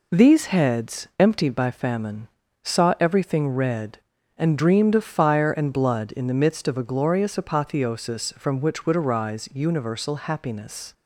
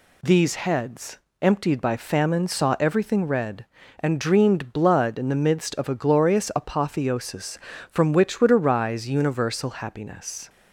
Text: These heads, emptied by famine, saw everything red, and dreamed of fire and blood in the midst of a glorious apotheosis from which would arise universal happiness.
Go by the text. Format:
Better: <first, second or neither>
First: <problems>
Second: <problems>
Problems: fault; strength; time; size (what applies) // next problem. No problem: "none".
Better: first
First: none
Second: skips "of fire and"; at 4.7 s